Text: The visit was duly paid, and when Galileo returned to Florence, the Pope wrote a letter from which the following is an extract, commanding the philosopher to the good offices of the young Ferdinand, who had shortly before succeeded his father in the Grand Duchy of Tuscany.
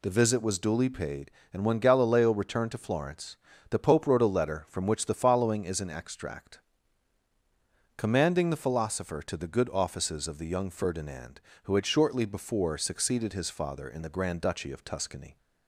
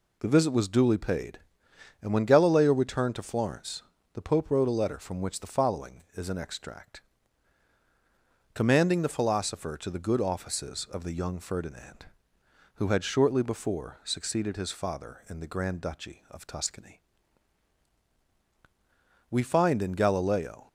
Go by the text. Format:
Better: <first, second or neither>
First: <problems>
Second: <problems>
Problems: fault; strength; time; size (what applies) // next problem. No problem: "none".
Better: first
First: none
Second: goes on to say "We find in Galileo"; from 19.2 s on; 1.3 s long